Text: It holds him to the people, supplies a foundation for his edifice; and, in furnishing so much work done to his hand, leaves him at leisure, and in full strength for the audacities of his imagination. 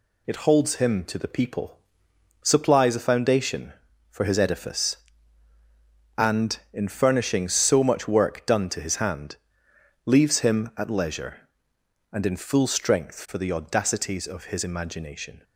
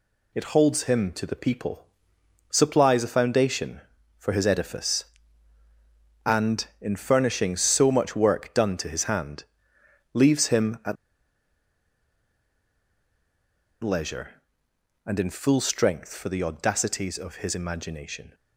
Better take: first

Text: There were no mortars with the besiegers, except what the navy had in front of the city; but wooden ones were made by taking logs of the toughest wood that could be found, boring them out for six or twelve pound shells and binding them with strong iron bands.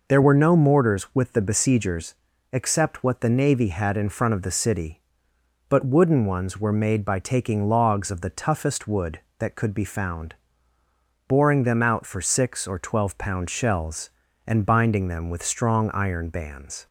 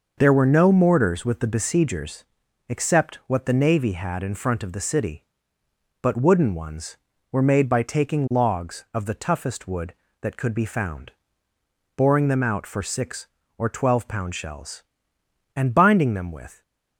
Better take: first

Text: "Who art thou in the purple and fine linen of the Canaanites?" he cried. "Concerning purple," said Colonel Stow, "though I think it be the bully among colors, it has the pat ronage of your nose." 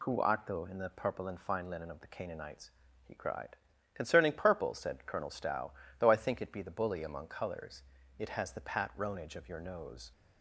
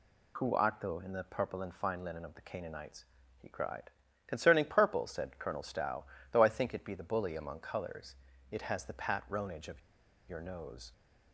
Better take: first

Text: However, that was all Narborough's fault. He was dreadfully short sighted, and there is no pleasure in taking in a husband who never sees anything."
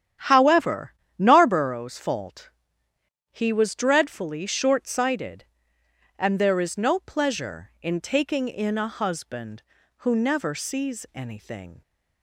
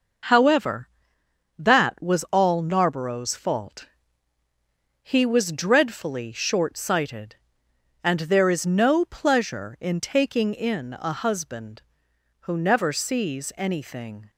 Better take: second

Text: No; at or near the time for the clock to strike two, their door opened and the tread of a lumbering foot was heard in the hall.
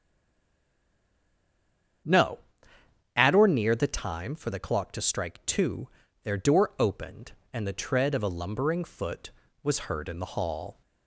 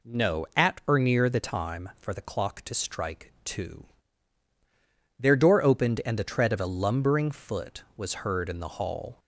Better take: second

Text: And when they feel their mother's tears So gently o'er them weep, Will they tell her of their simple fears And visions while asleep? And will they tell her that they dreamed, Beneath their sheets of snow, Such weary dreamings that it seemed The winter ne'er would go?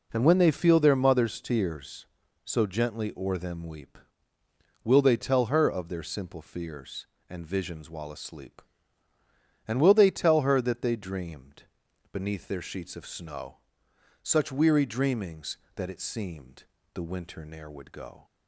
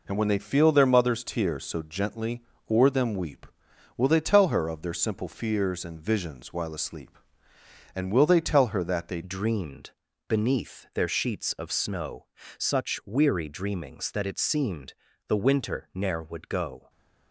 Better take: first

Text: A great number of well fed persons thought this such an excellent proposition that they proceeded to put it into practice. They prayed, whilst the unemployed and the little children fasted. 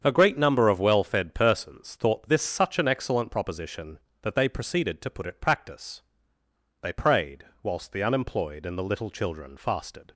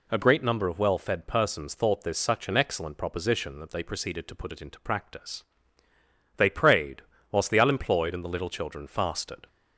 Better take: second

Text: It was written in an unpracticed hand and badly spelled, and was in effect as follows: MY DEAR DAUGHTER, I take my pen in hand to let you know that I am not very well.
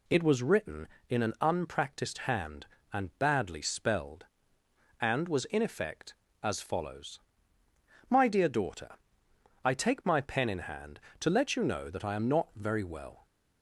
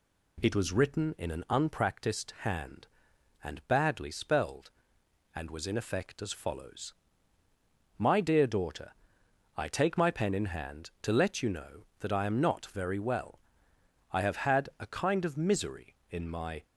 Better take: first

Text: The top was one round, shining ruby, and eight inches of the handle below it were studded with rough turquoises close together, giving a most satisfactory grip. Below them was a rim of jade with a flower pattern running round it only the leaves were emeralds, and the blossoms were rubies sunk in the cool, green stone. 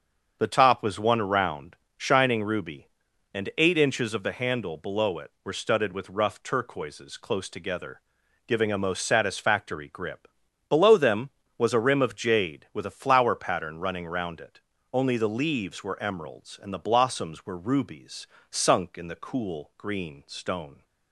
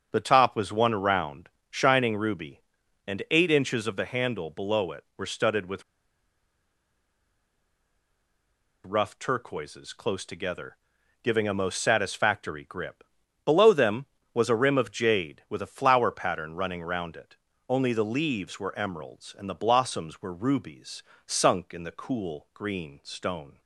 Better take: first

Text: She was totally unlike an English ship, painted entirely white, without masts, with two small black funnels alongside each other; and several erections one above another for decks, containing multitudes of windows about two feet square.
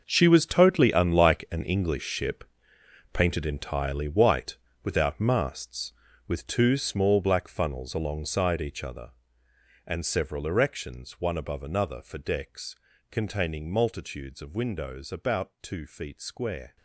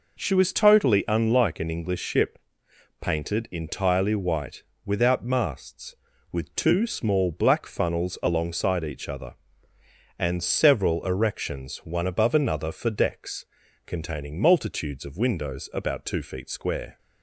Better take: second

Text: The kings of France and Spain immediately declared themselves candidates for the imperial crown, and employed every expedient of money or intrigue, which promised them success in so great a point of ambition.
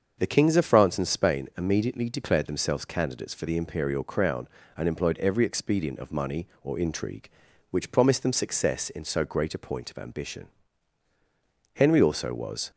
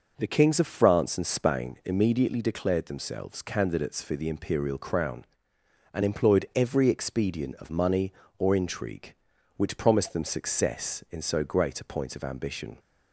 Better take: second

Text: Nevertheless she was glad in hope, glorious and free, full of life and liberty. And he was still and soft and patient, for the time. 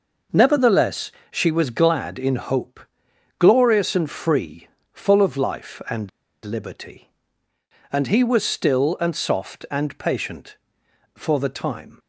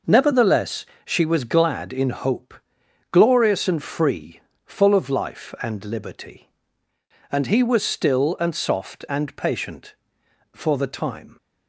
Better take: second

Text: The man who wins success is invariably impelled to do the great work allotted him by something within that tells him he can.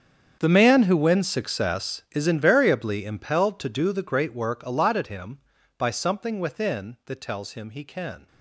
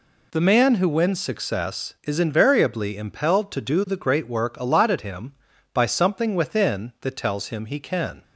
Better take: second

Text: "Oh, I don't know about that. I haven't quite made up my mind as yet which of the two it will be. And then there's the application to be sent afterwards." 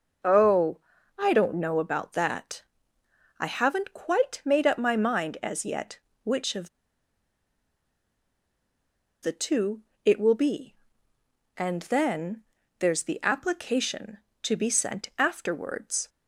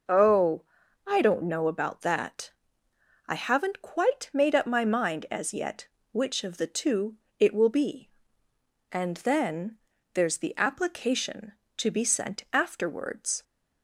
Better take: second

